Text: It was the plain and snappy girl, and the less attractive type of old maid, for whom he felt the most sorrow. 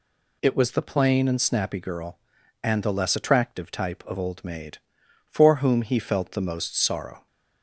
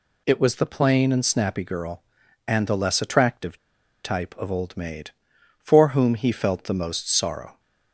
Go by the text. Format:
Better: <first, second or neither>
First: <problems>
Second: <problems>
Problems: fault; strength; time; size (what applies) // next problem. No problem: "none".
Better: first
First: none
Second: pauses between "attractive" and "type"; noticeable; at 3.5 s; 0.46 s long